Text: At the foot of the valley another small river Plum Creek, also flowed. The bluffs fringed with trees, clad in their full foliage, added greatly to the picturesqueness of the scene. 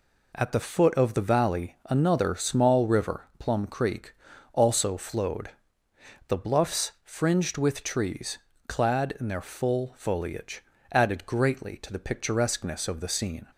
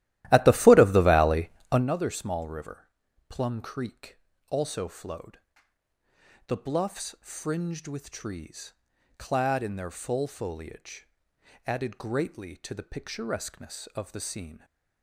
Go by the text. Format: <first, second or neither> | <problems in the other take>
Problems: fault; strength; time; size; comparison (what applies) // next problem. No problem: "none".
first | starts louder than the rest; strong; until 1.9 s; 14.5 dB // pauses between "valley" and "another"; slight; at 1.4 s; 0.20 s long // pauses between "river" and "Plum"; at 2.8 s; 0.40 s long